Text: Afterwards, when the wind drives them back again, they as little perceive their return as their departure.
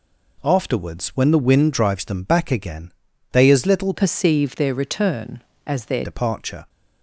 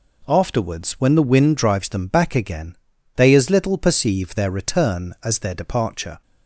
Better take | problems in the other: second | changes voice from "perceive" to "their"; from 3.9 to 6.0 s; 2.1 s long

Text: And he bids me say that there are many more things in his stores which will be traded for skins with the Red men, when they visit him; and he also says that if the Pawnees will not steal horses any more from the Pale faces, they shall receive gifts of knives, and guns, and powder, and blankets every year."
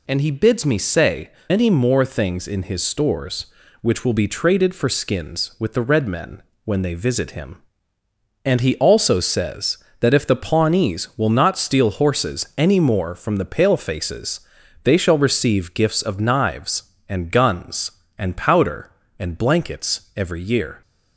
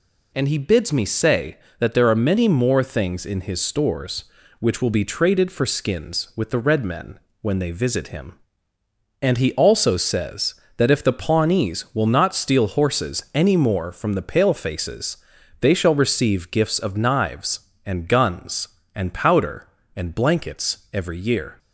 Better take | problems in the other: second | skips "that there are"; at 1.4 s

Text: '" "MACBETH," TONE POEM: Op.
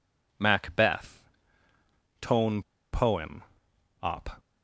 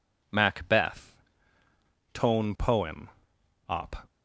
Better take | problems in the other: second | pauses between "TONE" and "POEM"; slight; at 2.6 s; 0.31 s long

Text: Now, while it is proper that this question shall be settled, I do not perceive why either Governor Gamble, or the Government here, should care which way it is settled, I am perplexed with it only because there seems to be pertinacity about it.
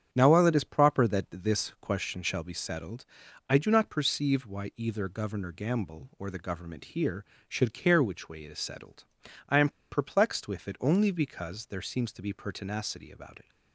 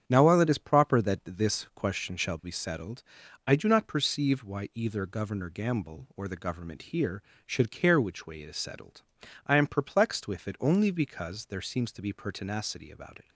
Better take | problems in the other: second | starts louder than the rest; strong; until 1.1 s; 8.5 dB; strong in the second // pauses between "am" and "perplexed"; slight; at 9.6 s; 0.20 s long

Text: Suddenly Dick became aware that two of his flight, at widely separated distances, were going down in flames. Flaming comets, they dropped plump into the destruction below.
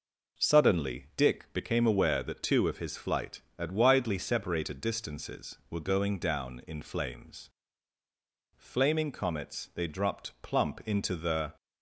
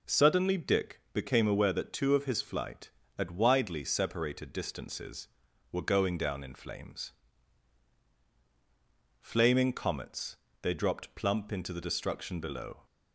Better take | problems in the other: second | stops before "destruction below"; at 11.5 s

